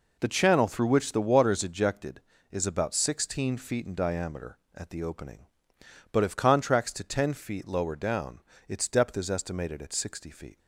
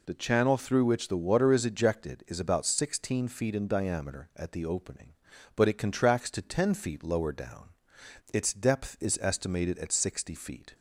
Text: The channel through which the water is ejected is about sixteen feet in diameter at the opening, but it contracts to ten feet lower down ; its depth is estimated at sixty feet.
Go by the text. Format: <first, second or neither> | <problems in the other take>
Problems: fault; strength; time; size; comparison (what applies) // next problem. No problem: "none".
second | says "if" for "it"; at 6.2 s